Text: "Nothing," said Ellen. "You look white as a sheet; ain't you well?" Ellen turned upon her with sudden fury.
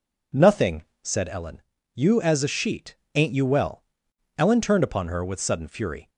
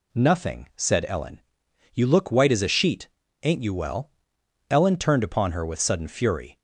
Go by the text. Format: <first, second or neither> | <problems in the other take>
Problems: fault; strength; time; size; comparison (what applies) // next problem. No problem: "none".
second | skips "look white"; at 2.1 s